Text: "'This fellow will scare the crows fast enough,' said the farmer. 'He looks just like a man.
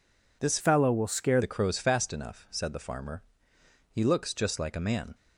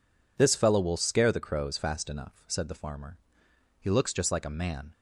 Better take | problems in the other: second | changes voice from "fellow" to "scare"; from 0.6 to 1.3 s; 0.7 s long

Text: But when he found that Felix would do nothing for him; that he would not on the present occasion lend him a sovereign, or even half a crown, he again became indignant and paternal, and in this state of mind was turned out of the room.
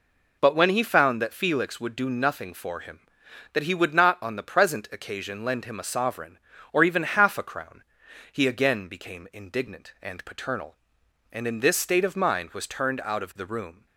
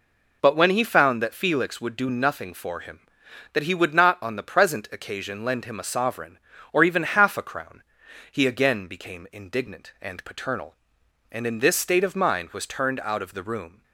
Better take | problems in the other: neither | none

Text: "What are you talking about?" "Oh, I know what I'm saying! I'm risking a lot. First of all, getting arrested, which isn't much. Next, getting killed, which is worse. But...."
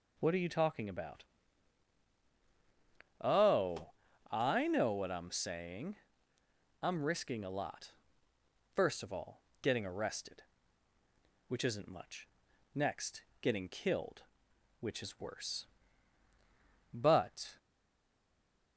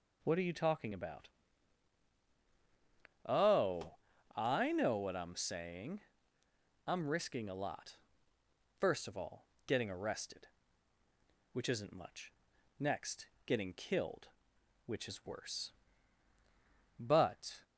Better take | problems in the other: second | stays silent after the last word; noticeable; from 17.5 s on; 1.2 s long

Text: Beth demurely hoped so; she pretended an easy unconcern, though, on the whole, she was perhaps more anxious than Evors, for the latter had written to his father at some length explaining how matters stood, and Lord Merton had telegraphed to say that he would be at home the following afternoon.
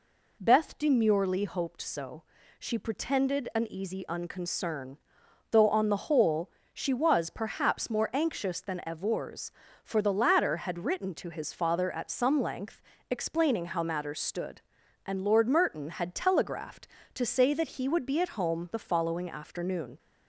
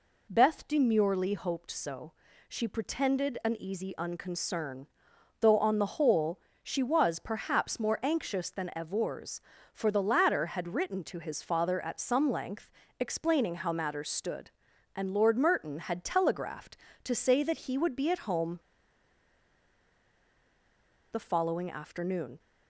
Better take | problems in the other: first | pauses between "length" and "explaining"; slight; at 12.7 s; 0.28 s long; slight in the first // pauses between "home" and "the"; strong; at 18.5 s; 2.5 s long

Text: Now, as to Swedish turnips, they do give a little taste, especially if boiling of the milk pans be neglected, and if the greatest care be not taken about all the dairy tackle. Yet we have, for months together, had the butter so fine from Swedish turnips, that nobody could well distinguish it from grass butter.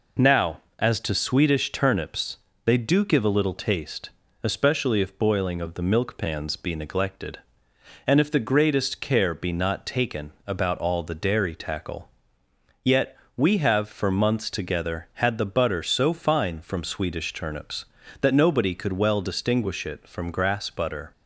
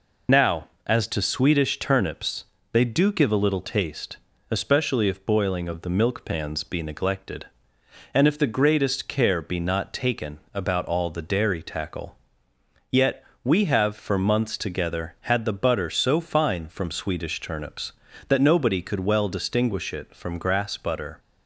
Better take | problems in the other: first | loses the start of "Now"; at 0.2 s; 55 ms // pauses between "taken" and "about"; slight; at 10.3 s; 0.16 s long; slight in the first // pauses between "Yet" and "we"; slight; at 13.2 s; 0.20 s long; slight in the first

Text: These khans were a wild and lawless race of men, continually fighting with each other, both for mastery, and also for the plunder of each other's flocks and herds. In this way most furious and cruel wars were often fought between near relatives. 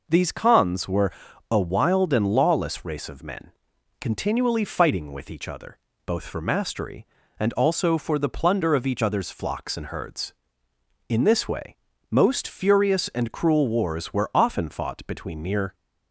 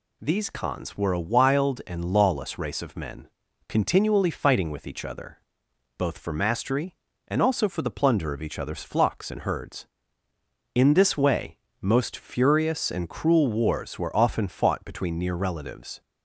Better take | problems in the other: second | pauses between "were" and "a"; at 1.1 s; 0.38 s long // pauses between "way" and "most"; slight; at 11.7 s; 0.34 s long; slight in the second // stops before "relatives"; at 15.7 s

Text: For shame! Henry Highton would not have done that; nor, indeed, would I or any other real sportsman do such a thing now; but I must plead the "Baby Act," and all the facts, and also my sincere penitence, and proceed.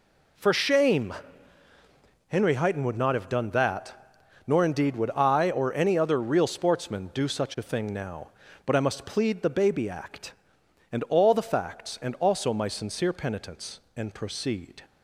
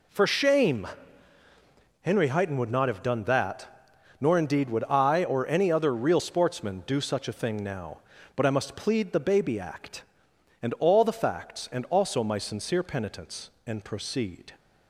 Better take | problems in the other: neither | none

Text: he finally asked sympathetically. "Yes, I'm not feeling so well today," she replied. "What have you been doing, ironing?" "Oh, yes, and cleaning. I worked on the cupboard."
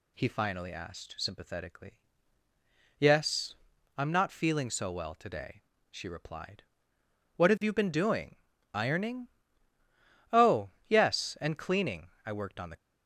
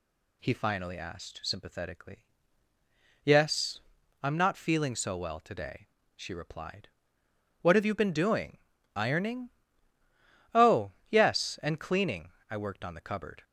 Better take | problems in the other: second | stops before "cupboard"; at 12.7 s

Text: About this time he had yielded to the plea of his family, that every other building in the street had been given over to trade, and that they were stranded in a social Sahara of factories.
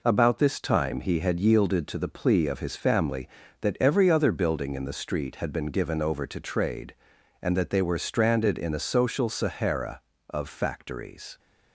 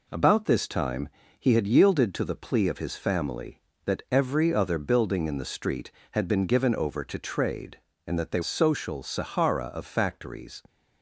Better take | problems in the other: first | pauses between "time" and "he"; slight; at 1.0 s; 0.28 s long // skips "were stranded in a"; at 8.4 s

